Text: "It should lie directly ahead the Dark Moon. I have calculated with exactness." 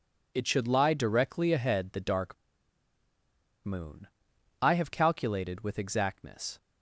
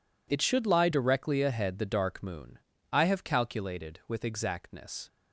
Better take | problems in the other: second | pauses between "Dark" and "Moon"; strong; at 2.3 s; 1.3 s long

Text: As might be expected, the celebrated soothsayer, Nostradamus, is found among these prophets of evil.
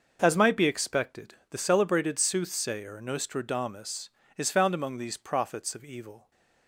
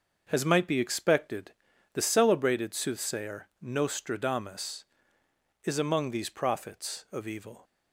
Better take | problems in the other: first | starts louder than the rest; noticeable; until 1.3 s; 6 dB; noticeable in the first // skips "found"; at 5.7 s

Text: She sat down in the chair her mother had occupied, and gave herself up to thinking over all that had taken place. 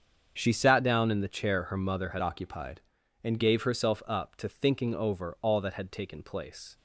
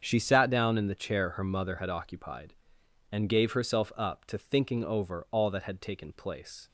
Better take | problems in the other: second | starts louder than the rest; strong; until 1.3 s; 7 dB; strong in the second // changes voice from "occupied" to "and"; from 2.2 to 3.3 s; 1.1 s long

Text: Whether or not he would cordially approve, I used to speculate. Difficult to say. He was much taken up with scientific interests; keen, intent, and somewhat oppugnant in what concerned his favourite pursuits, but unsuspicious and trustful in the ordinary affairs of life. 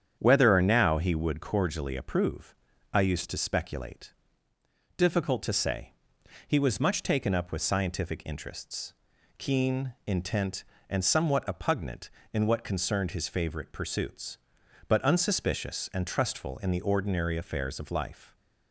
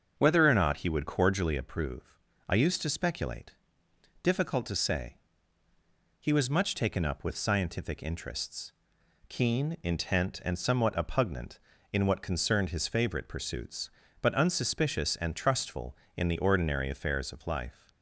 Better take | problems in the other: second | starts louder than the rest; strong; until 1.2 s; 8.5 dB; also in the second // says "now" for "not"; at 0.6 s

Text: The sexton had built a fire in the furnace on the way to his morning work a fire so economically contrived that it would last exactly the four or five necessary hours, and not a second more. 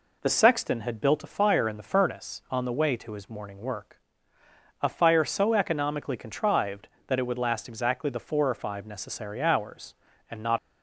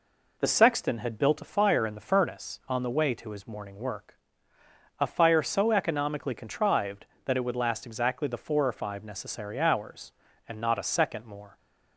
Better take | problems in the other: second | pauses between "work" and "a"; noticeable; at 4.0 s; 0.80 s long; noticeable in the second // stops before "a second more"; at 10.5 s

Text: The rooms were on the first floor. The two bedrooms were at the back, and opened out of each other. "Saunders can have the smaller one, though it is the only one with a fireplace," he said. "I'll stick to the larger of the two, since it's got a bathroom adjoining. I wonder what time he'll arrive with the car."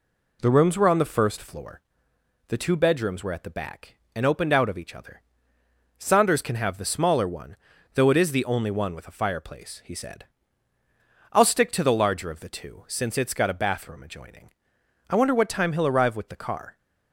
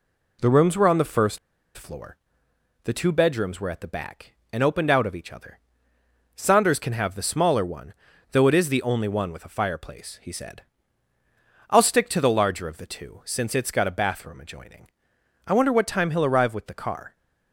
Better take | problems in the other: first | pauses between "first" and "floor"; at 1.3 s; 0.38 s long

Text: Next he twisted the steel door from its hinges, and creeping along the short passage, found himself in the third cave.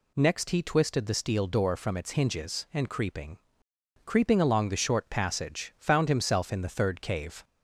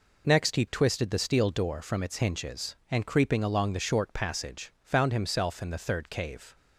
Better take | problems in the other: second | says "creeping" twice; at 4.0 s

